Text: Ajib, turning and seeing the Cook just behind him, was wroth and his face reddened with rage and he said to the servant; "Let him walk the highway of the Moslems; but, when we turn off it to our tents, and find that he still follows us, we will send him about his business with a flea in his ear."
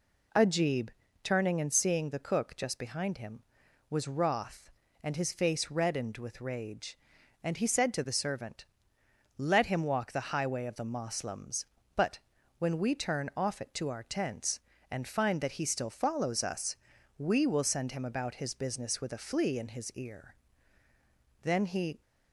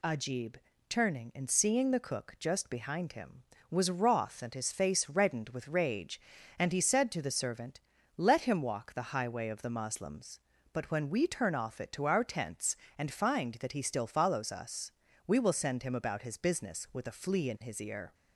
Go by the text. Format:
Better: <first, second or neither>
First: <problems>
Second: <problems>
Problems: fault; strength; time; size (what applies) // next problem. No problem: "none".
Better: second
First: goes on to say "Then he"; from 21.4 s on; 0.58 s long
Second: none